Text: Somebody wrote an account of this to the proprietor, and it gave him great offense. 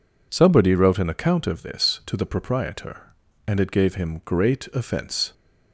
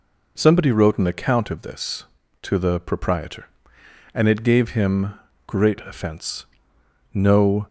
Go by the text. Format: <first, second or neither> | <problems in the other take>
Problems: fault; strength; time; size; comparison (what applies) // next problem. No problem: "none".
first | pauses between "him" and "great"; slight; at 5.1 s; 0.34 s long // goes on to say "No"; from 7.1 s on; 0.54 s long